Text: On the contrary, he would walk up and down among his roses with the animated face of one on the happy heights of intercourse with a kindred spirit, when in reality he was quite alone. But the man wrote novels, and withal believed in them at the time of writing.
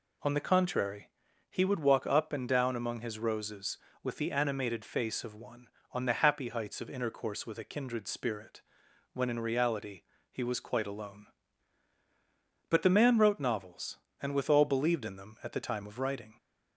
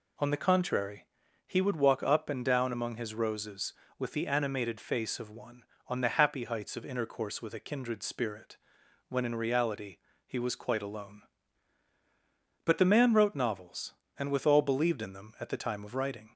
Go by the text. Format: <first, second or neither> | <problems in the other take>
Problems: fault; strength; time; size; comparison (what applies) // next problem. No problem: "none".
neither | pauses between "reality" and "he"; slight; the same in both